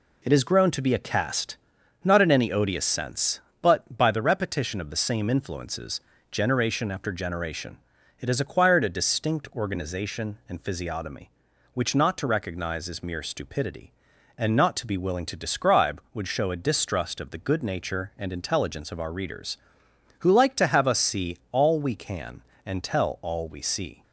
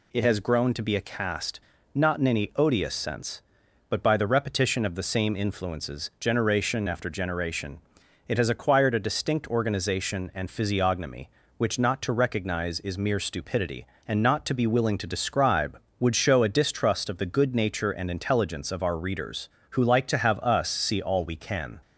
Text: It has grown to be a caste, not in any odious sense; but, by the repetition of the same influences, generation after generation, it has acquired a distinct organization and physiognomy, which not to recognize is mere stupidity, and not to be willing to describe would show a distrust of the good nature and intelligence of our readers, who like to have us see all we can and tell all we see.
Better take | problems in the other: first | stops before "and tell all we see"; at 21.8 s

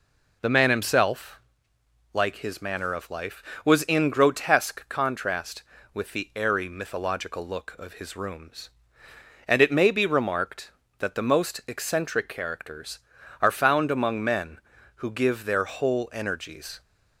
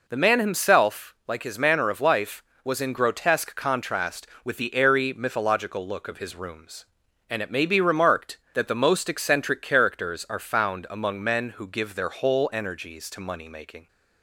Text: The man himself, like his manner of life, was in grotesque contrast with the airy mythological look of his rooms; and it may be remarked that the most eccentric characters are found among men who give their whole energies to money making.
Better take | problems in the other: second | stops before "to money making"; at 16.8 s

